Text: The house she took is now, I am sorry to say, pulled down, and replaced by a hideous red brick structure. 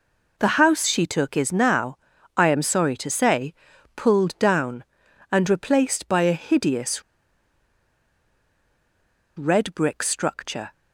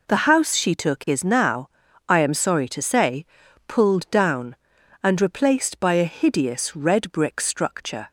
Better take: second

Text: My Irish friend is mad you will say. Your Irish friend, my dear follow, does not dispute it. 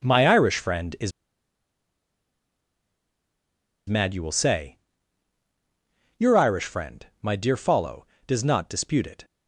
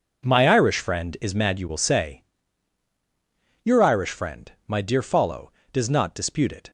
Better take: second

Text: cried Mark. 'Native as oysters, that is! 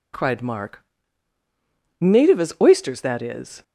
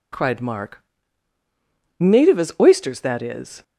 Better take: neither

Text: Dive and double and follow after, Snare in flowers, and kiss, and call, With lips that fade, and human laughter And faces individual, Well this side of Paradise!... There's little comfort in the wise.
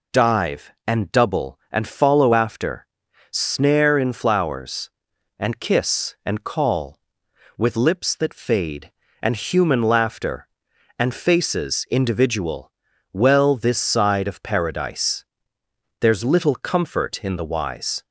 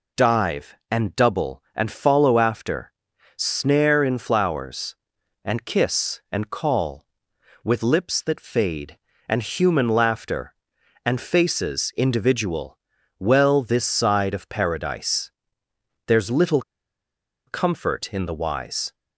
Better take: first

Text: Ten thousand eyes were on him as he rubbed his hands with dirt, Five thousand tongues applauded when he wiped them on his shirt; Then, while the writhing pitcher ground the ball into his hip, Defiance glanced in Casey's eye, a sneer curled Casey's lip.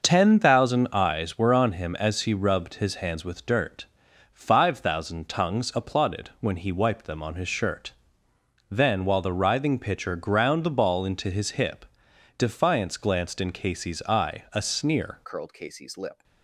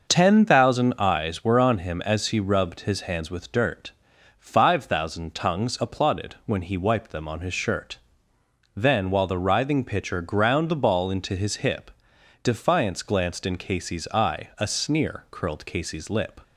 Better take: second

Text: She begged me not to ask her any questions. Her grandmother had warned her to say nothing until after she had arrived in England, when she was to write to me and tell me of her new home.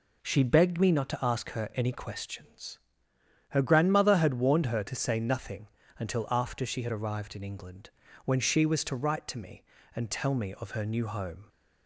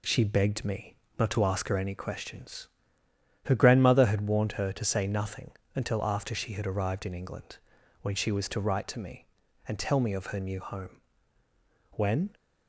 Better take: first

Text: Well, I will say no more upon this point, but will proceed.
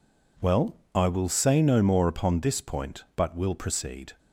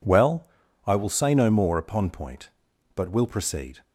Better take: first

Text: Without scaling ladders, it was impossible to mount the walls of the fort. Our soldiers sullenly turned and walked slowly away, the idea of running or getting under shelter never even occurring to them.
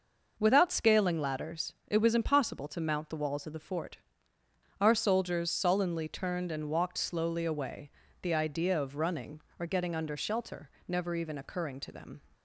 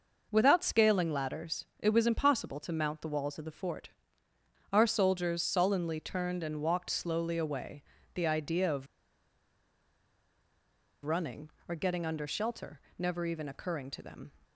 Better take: first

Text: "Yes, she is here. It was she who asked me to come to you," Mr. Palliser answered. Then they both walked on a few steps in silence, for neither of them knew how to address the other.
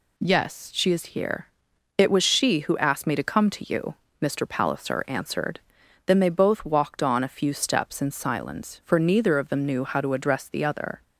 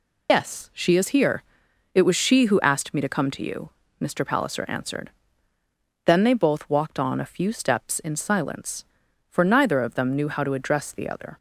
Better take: first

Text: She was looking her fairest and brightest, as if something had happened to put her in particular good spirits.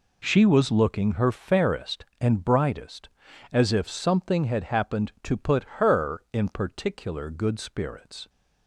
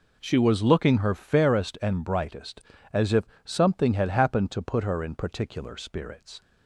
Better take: first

